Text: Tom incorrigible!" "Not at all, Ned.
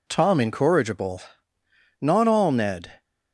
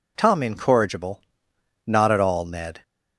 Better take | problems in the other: second | skips "at"; at 2.2 s

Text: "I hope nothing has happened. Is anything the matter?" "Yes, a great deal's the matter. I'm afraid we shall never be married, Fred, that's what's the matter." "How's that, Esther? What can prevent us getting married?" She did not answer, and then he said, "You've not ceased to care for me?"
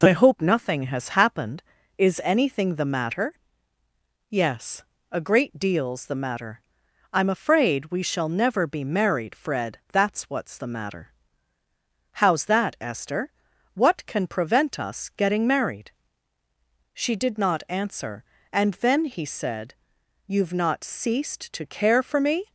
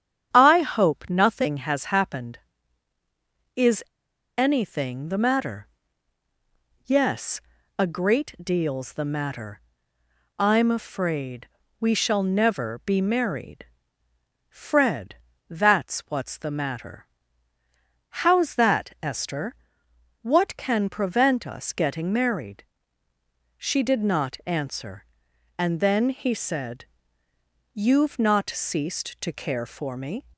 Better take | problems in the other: first | starts louder than the rest; strong; until 1.3 s; 9 dB // pauses between "Is" and "anything"; noticeable; at 3.8 s; 0.54 s long // pauses between "afraid" and "we"; slight; at 11.4 s; 0.32 s long

